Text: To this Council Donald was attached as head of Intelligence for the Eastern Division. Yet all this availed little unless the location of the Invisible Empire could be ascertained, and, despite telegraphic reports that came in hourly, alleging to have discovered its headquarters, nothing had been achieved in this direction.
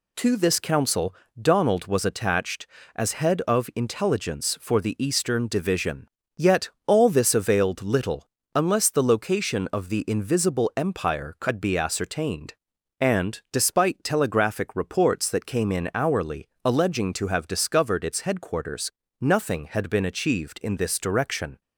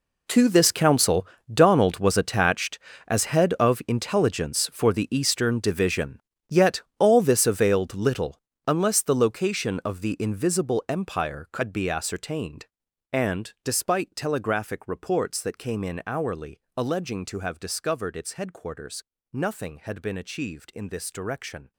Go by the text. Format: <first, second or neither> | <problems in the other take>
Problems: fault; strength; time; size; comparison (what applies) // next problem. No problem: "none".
first | gets quieter; strong; throughout; 16 dB // pauses between "Council" and "Donald"; slight; at 1.2 s; 0.26 s long; slight in the first // pauses between "Yet" and "all"; slight; at 6.8 s; 0.16 s long; slight in the first // pauses between "little" and "unless"; slight; at 8.3 s; 0.26 s long; slight in the first